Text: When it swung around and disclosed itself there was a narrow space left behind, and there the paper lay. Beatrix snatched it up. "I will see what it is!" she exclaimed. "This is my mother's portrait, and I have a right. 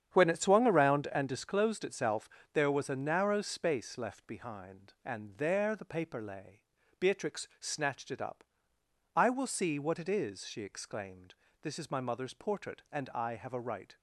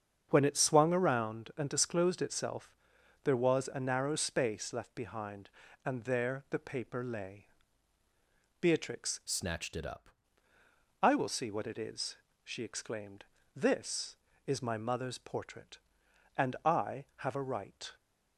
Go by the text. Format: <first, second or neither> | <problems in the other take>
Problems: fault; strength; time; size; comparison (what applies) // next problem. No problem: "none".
first | starts louder than the rest; strong; until 1.3 s; 7.5 dB; strong in the first // pauses between "itself" and "there"; noticeable; at 2.6 s; 0.54 s long; slight in the first // changes voice from "snatched" to "up"; from 9.2 to 10.0 s; 0.8 s long